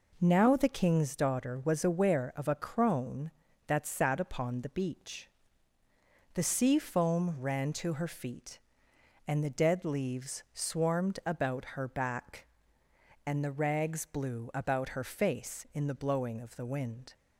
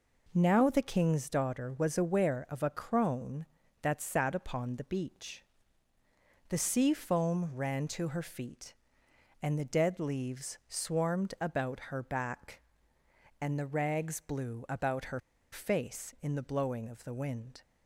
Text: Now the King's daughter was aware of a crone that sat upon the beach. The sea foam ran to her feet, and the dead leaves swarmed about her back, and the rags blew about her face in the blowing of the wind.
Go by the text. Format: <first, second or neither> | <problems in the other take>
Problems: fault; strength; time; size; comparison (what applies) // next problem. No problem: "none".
first | pauses between "her" and "face"; slight; at 15.1 s; 0.32 s long